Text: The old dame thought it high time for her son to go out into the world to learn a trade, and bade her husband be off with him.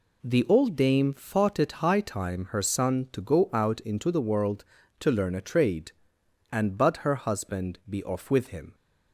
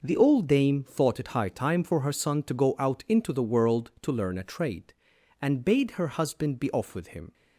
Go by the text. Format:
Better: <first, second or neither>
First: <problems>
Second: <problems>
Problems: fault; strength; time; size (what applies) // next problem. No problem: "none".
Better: second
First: skips "for"; at 2.4 s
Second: none